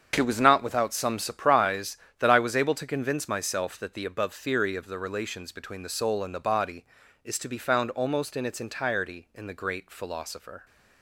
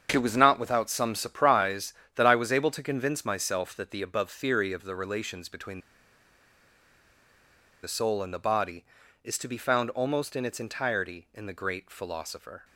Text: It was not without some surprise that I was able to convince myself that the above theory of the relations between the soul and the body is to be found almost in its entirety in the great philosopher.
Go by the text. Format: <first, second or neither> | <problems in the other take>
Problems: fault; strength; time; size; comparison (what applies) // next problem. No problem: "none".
first | starts louder than the rest; strong; until 1.1 s; 7.5 dB; strong in the first // pauses between "between" and "the"; strong; at 5.7 s; 2.0 s long